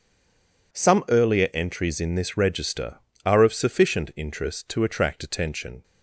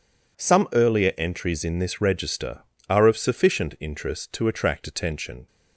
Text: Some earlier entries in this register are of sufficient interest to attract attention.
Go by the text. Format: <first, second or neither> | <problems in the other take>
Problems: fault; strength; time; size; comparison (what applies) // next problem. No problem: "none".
second | stays silent before the first word; slight; until 0.7 s; 0.7 s long